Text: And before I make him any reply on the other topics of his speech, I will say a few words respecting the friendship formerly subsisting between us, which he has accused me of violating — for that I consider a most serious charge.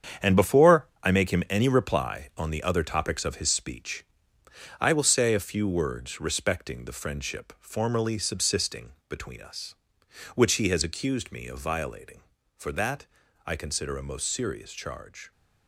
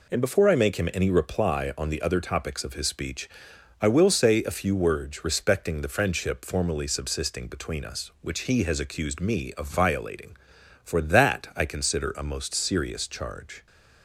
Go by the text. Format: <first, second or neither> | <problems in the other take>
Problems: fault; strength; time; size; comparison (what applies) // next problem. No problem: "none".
second | gets quieter; strong; throughout; 9 dB // pauses between "before" and "I"; slight; at 0.8 s; 0.16 s long // pauses between "subsisting" and "between"; slight; at 8.9 s; 0.16 s long // pauses between "that" and "I"; at 13.0 s; 0.38 s long